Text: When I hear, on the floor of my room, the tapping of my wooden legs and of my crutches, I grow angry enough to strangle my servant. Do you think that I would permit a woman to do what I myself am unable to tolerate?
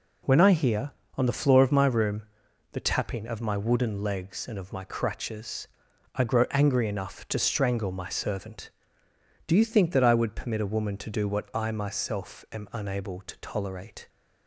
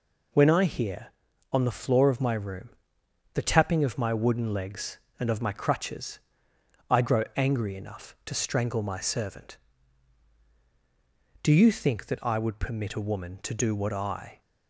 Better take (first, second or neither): first